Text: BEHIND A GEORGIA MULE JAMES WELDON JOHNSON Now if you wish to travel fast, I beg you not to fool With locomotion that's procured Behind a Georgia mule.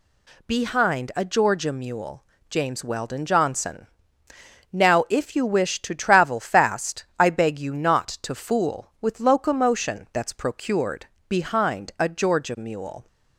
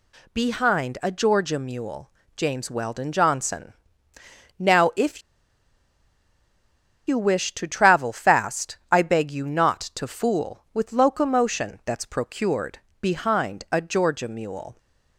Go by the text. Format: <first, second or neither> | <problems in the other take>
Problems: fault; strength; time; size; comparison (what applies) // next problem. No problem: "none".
first | pauses between "MULE" and "JAMES"; slight; at 2.1 s; 0.24 s long; slight in the first // pauses between "JOHNSON" and "Now"; noticeable; at 3.7 s; 0.86 s long; noticeable in the first // pauses between "if" and "you"; strong; at 5.2 s; 1.8 s long // pauses between "procured" and "Behind"; slight; at 12.7 s; 0.24 s long; slight in the first